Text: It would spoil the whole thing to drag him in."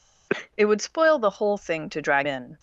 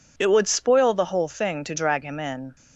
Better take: second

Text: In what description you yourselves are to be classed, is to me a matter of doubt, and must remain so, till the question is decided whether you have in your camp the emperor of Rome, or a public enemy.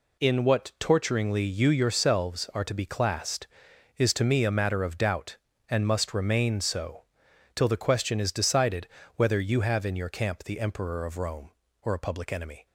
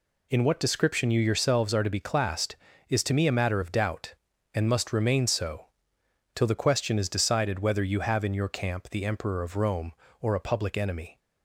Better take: second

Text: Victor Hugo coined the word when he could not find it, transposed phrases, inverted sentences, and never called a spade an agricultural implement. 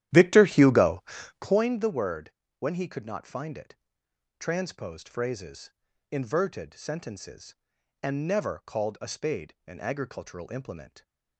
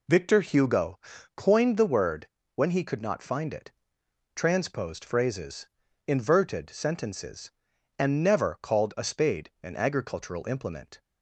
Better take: second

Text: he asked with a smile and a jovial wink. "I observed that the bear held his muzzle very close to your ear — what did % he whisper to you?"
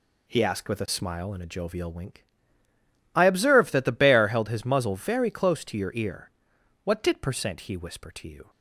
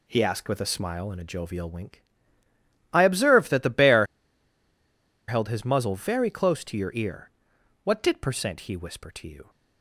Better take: first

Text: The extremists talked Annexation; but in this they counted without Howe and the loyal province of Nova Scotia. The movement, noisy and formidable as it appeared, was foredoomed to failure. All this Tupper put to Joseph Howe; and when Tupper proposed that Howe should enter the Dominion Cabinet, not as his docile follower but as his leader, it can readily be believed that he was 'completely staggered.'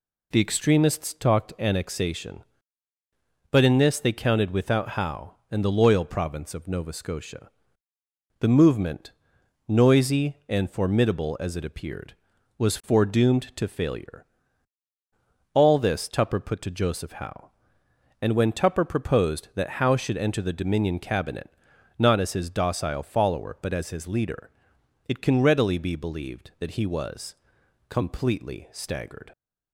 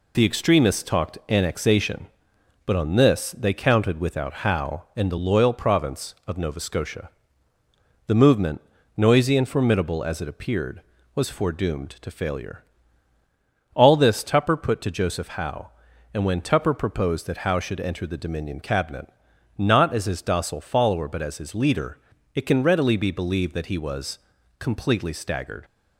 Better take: first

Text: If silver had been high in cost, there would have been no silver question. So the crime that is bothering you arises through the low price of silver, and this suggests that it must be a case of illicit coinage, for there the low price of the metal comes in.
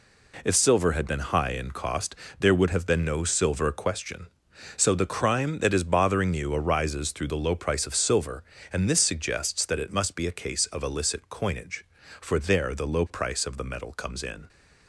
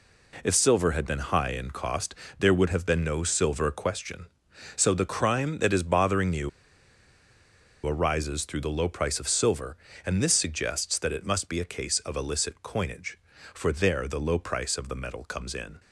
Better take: first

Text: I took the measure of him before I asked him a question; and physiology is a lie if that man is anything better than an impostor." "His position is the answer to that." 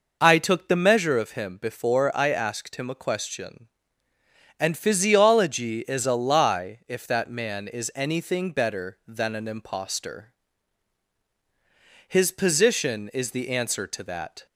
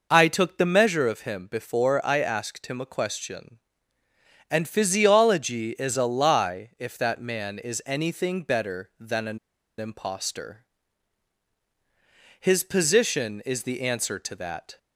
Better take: first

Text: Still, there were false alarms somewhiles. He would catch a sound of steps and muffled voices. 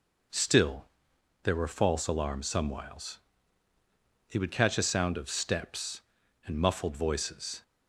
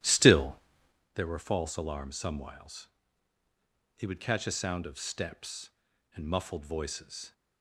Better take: first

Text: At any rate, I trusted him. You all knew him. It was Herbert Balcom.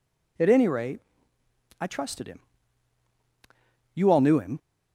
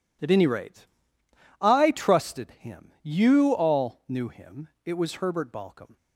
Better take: second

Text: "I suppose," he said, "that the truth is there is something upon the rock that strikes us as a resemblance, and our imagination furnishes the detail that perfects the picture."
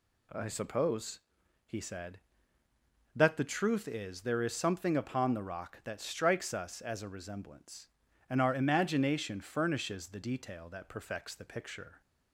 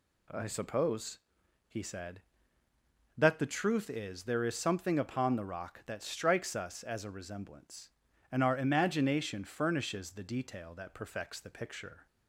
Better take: neither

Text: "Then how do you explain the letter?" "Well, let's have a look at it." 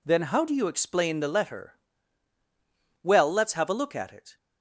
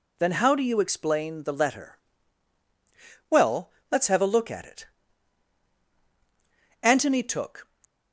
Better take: first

